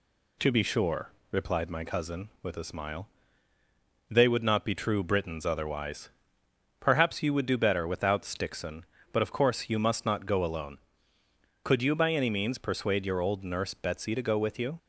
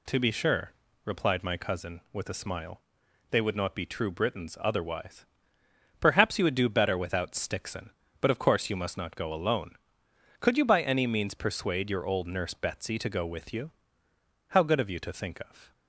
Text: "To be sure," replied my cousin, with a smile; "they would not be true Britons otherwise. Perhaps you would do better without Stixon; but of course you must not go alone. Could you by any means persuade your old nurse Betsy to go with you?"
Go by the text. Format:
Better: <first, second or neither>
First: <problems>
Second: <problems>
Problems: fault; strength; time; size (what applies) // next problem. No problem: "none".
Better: first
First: none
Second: goes on to say "How good of you to think of"; noticeable; from 14.4 s on; 1.2 s long